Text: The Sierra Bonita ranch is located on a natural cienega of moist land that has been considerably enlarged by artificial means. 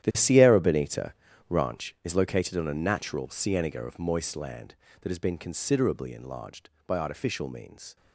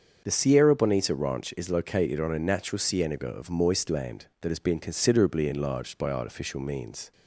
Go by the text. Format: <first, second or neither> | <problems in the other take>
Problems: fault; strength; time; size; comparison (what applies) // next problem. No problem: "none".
second | gets quieter; strong; throughout; 13.5 dB // starts louder than the rest; strong; until 1.0 s; 11 dB; also in the second // pauses between "Bonita" and "ranch"; slight; at 1.1 s; 0.34 s long